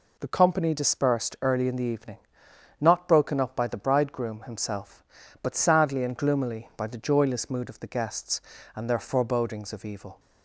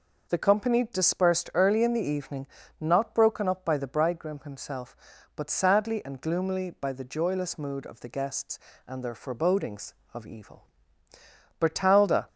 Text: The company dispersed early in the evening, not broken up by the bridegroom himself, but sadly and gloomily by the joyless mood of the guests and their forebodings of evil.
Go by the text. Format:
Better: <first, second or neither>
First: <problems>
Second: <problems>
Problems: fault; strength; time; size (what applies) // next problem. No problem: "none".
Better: first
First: none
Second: goes on to say "Bertalda"; noticeable; from 11.5 s on; 0.68 s long